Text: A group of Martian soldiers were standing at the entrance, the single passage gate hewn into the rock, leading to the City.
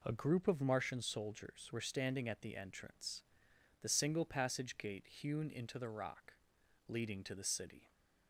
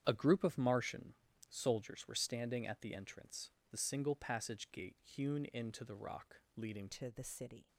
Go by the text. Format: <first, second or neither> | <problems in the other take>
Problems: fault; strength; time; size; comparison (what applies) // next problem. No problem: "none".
first | starts louder than the rest; strong; until 1.0 s; 9 dB // pauses between "Martian" and "soldiers"; slight; at 1.1 s; 0.36 s long // changes voice at "to"; from 6.8 s on; 0.8 s long